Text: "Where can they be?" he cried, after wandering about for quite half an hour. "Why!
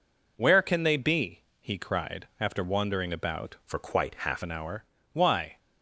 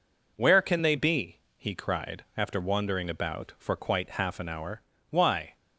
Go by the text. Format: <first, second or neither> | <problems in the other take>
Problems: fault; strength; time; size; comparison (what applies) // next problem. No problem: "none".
second | changes voice from "for" to "half"; from 3.6 to 4.4 s; 0.8 s long